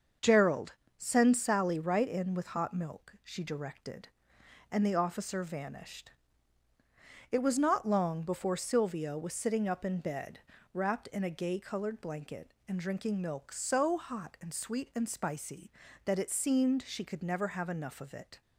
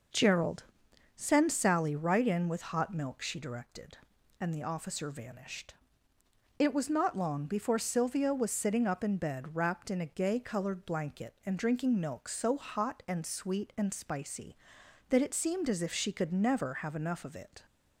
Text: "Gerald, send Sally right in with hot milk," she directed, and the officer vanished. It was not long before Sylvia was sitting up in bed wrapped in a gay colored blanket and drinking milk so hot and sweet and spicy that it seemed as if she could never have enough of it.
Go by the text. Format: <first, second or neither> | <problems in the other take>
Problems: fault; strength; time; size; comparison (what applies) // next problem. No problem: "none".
second | starts louder than the rest; until 1.4 s; 6.5 dB // pauses between "bed" and "wrapped"; slight; at 10.4 s; 0.32 s long // skips "as if"; at 16.8 s